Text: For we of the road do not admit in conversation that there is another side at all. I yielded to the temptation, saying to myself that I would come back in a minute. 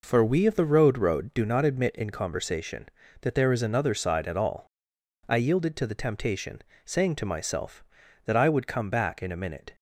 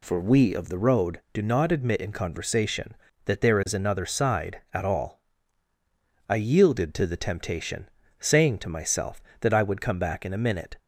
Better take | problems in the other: second | says "road" twice; at 0.9 s

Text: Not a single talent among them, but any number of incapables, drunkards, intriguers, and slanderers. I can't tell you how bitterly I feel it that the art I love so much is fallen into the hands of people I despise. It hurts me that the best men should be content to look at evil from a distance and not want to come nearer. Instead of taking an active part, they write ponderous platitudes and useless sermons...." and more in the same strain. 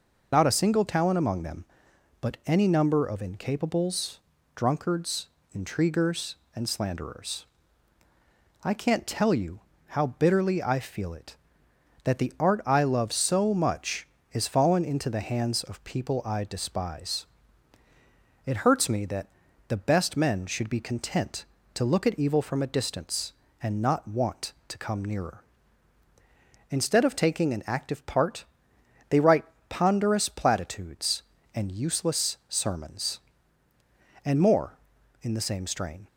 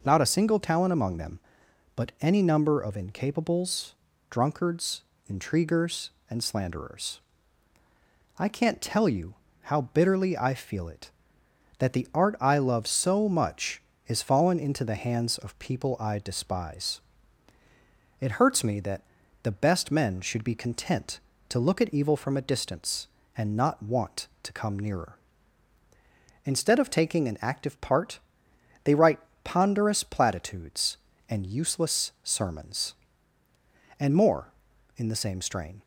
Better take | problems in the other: second | loses the start of "Not"; at 0.3 s; 60 ms // pauses between "you" and "how"; slight; at 9.6 s; 0.28 s long; slight in the second // pauses between "that" and "the"; at 19.2 s; 0.40 s long; also in the second // pauses between "write" and "ponderous"; slight; at 29.4 s; 0.24 s long; slight in the second

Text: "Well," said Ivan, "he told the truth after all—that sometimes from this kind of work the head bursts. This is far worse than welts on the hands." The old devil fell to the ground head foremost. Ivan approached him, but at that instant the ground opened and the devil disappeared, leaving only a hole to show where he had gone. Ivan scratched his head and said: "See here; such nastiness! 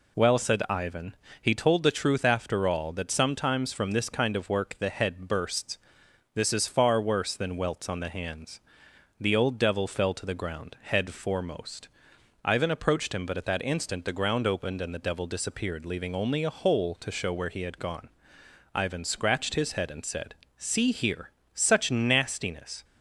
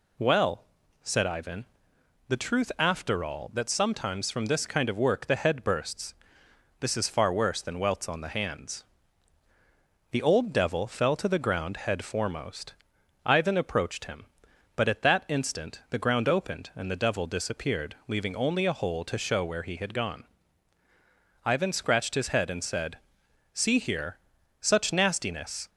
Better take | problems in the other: first | skips "he told"; at 1.9 s

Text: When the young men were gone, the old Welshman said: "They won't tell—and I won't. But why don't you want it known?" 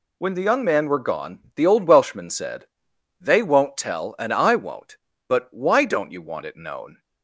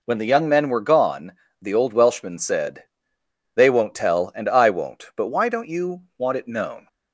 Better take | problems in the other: second | says "man" for "men"; at 0.6 s

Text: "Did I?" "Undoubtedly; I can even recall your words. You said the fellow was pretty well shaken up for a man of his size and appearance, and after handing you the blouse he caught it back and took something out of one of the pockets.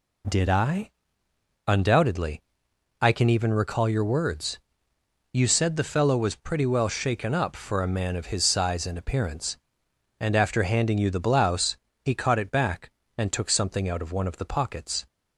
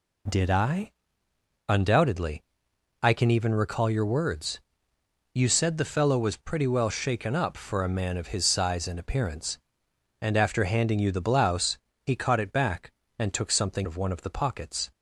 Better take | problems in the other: first | pauses between "blouse" and "he"; slight; at 11.7 s; 0.24 s long; slight in the first // skips "out"; at 13.8 s

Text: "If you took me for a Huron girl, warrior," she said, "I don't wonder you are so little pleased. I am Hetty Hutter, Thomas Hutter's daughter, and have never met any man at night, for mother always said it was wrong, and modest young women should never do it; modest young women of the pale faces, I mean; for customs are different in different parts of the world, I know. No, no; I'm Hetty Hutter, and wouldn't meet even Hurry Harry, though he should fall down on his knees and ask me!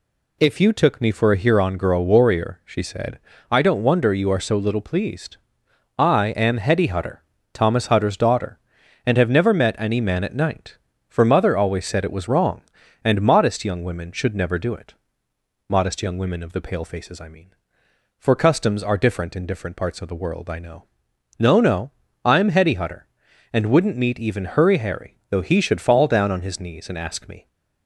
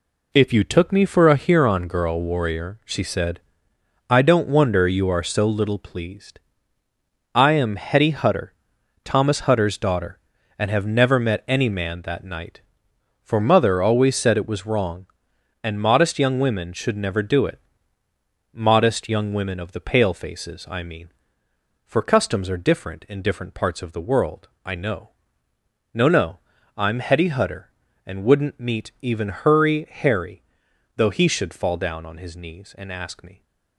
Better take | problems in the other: first | says "that" for "at"; at 12.0 s

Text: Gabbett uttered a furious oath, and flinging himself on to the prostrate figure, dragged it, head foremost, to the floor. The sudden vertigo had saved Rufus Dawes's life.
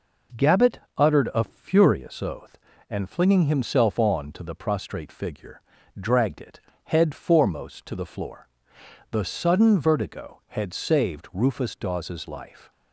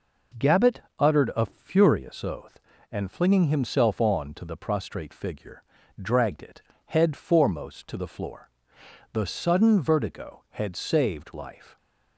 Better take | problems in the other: first | pauses between "Gabbett" and "uttered"; slight; at 0.8 s; 0.18 s long; slight in the first // skips "Rufus Dawes's"; at 11.3 s

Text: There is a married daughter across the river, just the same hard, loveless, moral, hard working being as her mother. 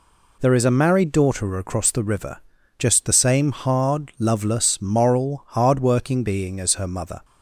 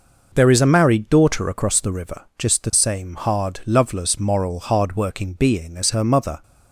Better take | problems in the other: neither | none

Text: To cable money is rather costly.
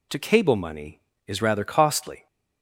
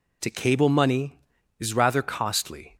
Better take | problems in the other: neither | none

